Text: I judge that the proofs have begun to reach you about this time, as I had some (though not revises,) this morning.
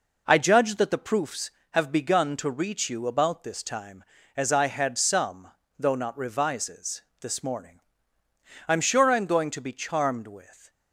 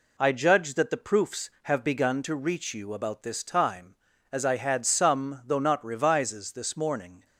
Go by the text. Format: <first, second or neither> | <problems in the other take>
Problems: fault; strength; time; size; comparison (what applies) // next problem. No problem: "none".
second | goes on to say "I'm sure I'm going to be charmed with"; strong; from 8.6 s on; 2.0 s long